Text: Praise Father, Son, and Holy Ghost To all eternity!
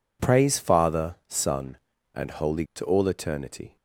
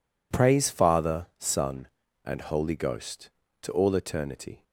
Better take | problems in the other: second | skips "Ghost"; at 2.7 s

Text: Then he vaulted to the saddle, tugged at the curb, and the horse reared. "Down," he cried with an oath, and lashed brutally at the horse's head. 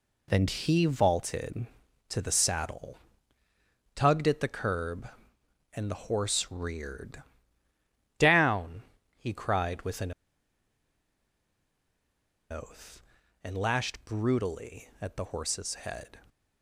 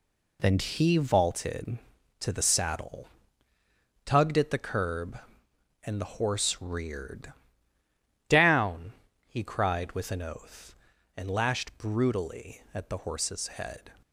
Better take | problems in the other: second | pauses between "an" and "oath"; strong; at 10.1 s; 2.3 s long

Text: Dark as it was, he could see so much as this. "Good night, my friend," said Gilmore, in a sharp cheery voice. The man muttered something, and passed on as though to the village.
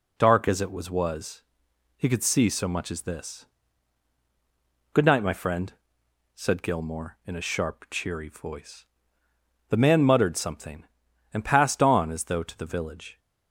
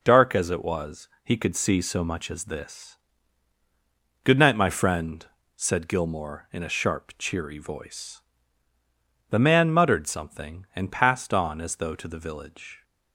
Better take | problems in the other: second | says "was" twice; at 0.9 s

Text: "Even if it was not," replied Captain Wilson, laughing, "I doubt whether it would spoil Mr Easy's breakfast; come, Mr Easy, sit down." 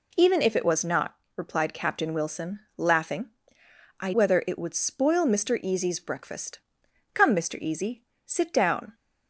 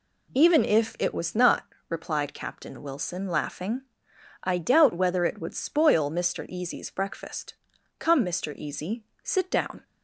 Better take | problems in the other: second | skips "doubt"; at 4.1 s

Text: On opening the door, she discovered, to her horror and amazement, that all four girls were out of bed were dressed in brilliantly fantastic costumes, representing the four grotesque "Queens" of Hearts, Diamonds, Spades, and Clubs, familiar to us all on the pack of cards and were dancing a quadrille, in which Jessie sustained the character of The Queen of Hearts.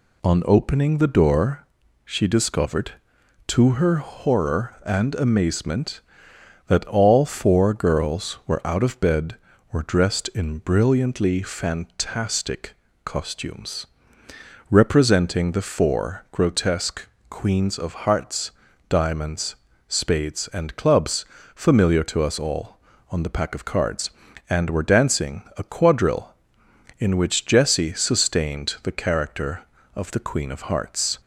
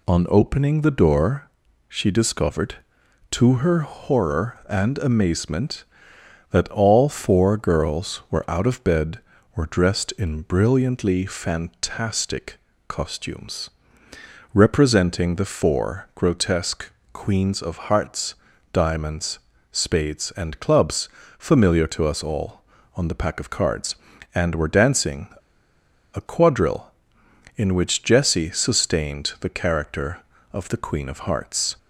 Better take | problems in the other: first | pauses between "fantastic" and "costumes"; slight; at 12.5 s; 0.32 s long; slight in the first // pauses between "grotesque" and "Queens"; slight; at 16.9 s; 0.22 s long; slight in the first // pauses between "dancing" and "a"; noticeable; at 25.2 s; 0.86 s long

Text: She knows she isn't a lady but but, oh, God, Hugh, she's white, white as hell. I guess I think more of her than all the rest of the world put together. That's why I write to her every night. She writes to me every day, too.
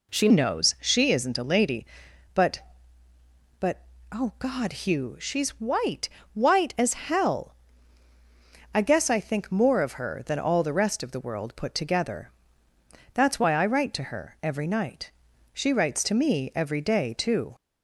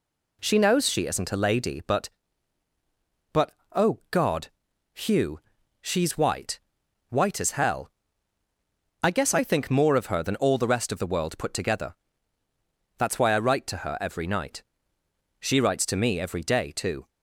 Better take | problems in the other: second | changes voice at "knows"; from 0.2 s on; 17.3 s long

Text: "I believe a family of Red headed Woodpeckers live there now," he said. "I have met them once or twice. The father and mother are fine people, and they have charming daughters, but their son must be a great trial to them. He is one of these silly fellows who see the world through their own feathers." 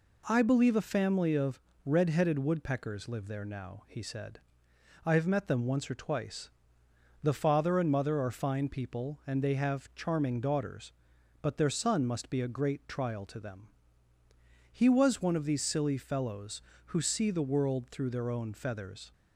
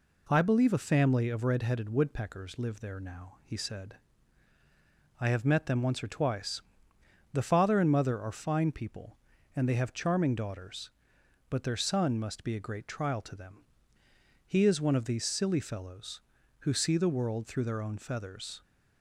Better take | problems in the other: second | pauses between "of" and "Red"; slight; at 1.6 s; 0.24 s long // says "was" for "is"; at 14.8 s

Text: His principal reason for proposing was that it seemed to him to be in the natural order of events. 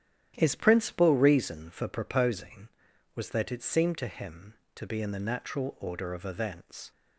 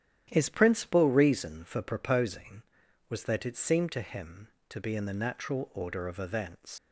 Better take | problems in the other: first | starts louder than the rest; strong; until 1.3 s; 11 dB; strong in the first // leaves "events" unfinished; at 6.7 s; 65 ms

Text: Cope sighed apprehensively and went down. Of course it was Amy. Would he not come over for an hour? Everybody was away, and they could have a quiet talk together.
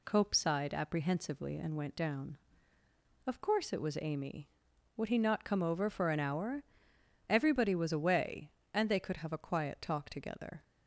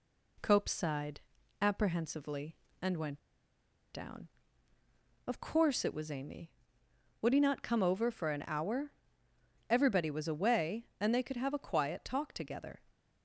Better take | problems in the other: first | pauses between "sighed" and "apprehensively"; at 1.2 s; 0.40 s long // pauses between "went" and "down"; noticeable; at 3.1 s; 0.74 s long

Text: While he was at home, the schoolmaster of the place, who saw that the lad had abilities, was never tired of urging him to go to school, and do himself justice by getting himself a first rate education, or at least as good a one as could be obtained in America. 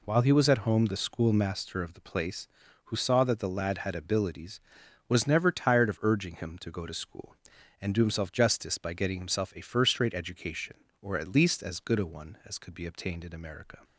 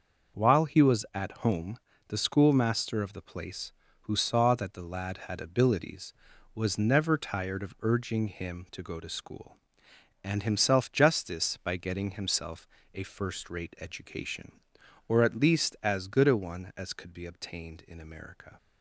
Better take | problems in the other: first | skips "do"; at 10.4 s // pauses between "himself" and "a"; slight; at 12.6 s; 0.26 s long

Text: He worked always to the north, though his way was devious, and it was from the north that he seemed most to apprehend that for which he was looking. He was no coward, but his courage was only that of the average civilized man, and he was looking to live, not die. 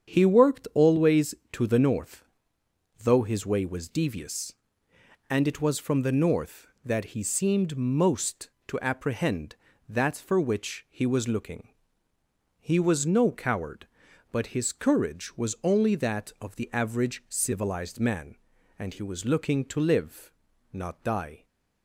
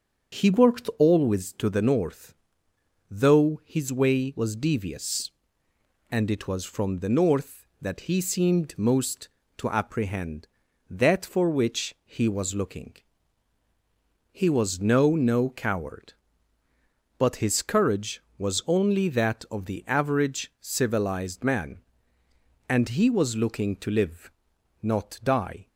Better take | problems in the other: first | starts louder than the rest; until 1.4 s; 7 dB; strong in the first // says "no" twice; at 15.1 s

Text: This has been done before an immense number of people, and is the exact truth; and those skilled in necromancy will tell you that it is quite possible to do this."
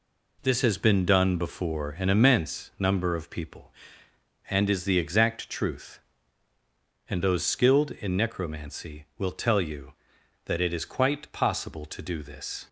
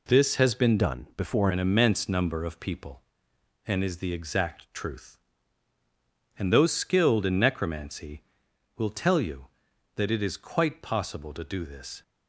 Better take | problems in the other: first | changes voice from "done" to "before"; from 0.7 to 1.4 s; 0.7 s long

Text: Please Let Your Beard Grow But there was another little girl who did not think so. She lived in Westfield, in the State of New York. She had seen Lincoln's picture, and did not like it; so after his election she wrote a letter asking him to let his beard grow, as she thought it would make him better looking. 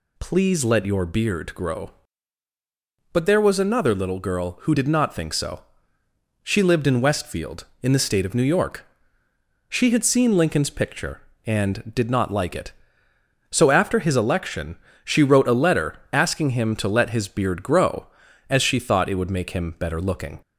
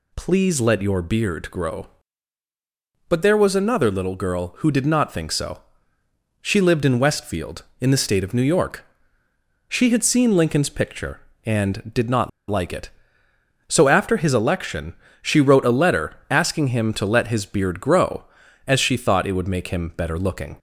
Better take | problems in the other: first | pauses between "not" and "like"; slight; at 12.2 s; 0.20 s long // pauses between "election" and "she"; slight; at 14.9 s; 0.26 s long; slight in the first

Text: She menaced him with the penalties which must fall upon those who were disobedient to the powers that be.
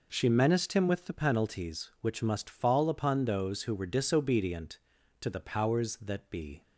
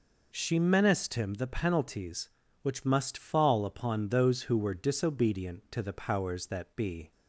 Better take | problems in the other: first | skips "with"; at 1.3 s

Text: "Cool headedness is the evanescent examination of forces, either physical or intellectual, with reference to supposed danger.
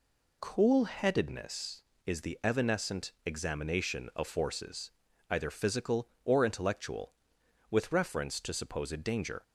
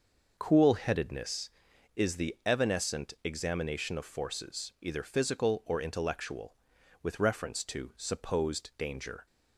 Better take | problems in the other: neither | none

